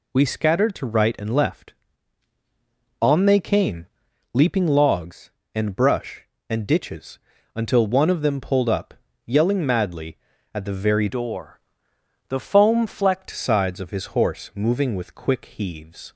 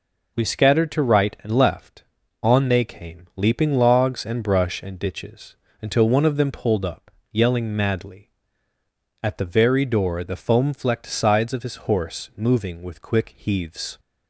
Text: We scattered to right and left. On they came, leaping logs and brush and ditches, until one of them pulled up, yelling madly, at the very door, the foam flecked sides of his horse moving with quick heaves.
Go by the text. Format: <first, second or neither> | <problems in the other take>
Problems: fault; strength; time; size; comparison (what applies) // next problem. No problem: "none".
second | changes voice from "door" to "flecked"; from 11.0 to 13.2 s; 2.2 s long